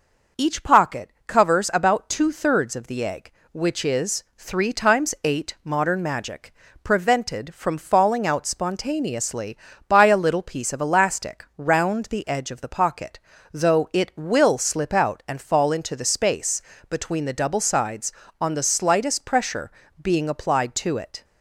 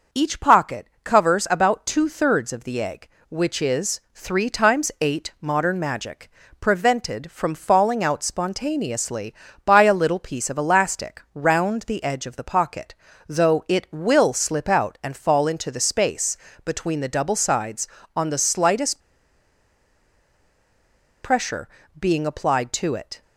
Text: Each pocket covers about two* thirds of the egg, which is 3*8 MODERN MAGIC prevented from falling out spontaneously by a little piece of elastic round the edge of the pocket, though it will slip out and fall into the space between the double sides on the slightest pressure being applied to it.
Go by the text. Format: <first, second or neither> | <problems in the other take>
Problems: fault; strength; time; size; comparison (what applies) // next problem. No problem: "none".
first | pauses between "pocket" and "covers"; slight; at 0.8 s; 0.18 s long; slight in the first // pauses between "MAGIC" and "prevented"; slight; at 6.2 s; 0.30 s long; slight in the first // pauses between "space" and "between"; slight; at 16.3 s; 0.30 s long; slight in the first // pauses between "slightest" and "pressure"; strong; at 18.9 s; 2.2 s long // pauses between "pressure" and "being"; slight; at 21.6 s; 0.32 s long; slight in the first